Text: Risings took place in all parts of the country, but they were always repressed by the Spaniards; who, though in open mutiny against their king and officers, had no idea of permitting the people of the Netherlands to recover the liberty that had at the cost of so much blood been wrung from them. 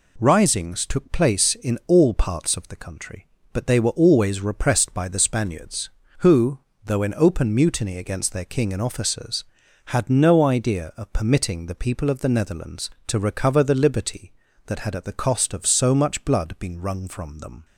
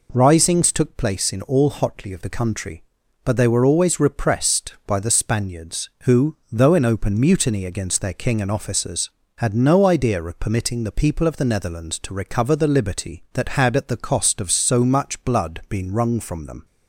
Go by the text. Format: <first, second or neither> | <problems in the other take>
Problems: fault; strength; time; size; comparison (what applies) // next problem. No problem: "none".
first | says "hotly" for "parts"; at 1.6 s